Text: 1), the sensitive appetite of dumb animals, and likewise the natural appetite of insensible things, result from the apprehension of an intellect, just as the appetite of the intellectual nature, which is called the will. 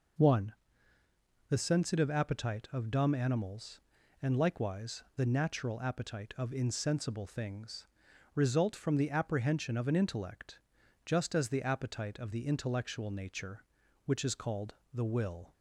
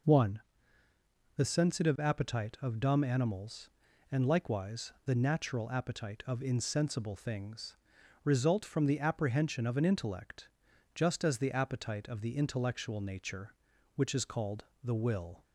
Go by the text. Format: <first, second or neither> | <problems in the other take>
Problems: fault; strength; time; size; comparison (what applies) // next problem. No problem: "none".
neither | pauses between "called" and "the"; slight; the same in both